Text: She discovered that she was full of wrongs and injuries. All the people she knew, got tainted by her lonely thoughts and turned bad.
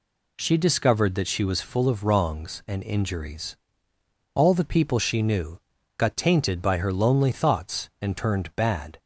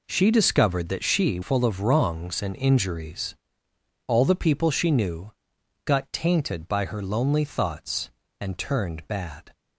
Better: first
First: none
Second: skips "was"; at 1.4 s

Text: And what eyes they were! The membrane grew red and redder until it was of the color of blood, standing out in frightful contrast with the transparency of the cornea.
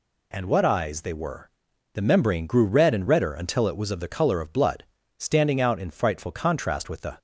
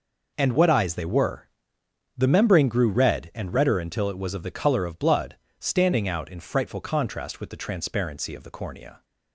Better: second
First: stops before "transparency of the cornea"; at 7.1 s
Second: none

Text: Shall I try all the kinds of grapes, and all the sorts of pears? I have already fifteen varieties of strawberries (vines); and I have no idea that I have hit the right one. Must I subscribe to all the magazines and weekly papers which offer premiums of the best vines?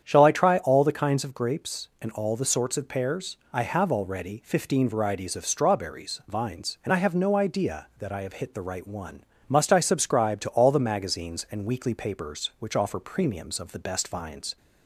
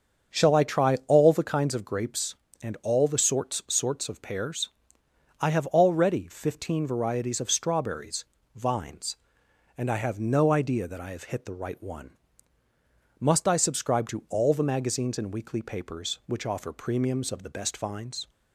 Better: first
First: starts louder than the rest; strong; until 1.0 s; 8.5 dB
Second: starts louder than the rest; until 1.4 s; 7 dB // says "sorts" twice; at 3.6 s

